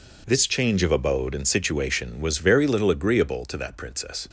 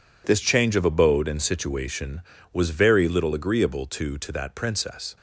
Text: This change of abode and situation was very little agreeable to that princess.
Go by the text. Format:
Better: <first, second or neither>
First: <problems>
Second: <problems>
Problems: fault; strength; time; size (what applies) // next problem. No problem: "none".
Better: first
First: none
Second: says "to" twice; at 4.1 s